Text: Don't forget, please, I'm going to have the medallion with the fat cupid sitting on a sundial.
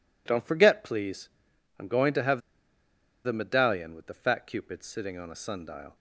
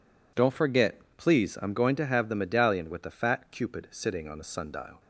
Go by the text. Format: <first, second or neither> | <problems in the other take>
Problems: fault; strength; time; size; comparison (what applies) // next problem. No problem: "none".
second | pauses between "have" and "the"; noticeable; at 2.4 s; 0.84 s long